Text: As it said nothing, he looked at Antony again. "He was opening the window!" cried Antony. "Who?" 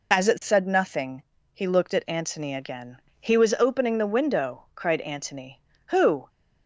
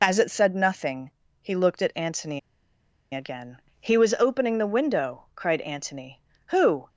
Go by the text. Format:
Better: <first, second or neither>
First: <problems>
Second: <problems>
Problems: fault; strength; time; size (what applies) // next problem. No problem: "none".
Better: first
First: none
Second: pauses between "Antony" and "again"; noticeable; at 2.3 s; 0.74 s long